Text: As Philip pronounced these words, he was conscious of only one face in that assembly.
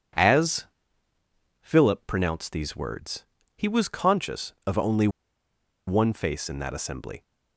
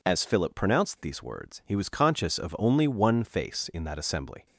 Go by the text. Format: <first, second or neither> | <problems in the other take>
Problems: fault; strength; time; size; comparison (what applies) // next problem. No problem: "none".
second | pauses between "As" and "Philip"; noticeable; at 0.6 s; 0.94 s long // pauses between "only" and "one"; noticeable; at 5.0 s; 0.79 s long